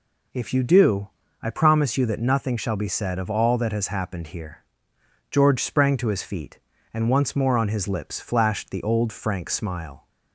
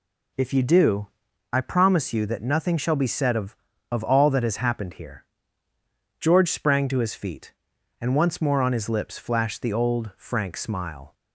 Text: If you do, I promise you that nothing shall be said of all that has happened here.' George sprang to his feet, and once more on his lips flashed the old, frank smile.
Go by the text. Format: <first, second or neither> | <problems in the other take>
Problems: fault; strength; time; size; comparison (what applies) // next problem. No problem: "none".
first | says "of" twice; at 3.9 s